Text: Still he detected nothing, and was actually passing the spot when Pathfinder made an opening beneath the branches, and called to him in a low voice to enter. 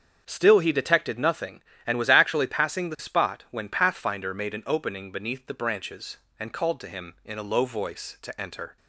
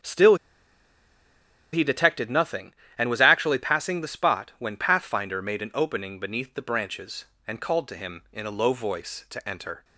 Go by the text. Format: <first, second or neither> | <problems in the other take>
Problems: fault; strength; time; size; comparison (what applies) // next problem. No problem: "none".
first | starts louder than the rest; strong; until 2.4 s; 7.5 dB; strong in the first // pauses between "Still" and "he"; strong; at 0.3 s; 1.3 s long